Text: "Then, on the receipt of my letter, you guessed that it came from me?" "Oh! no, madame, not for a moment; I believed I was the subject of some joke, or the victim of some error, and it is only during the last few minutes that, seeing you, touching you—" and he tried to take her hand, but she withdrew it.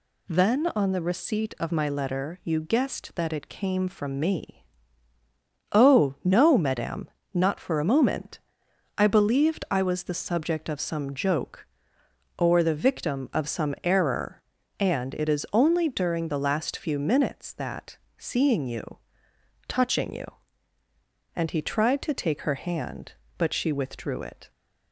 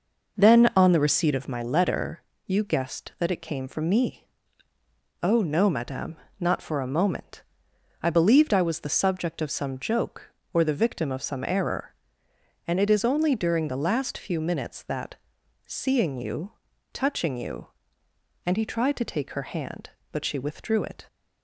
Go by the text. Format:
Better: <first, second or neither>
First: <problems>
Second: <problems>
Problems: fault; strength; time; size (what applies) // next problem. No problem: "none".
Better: first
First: none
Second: starts louder than the rest; noticeable; until 1.4 s; 5.5 dB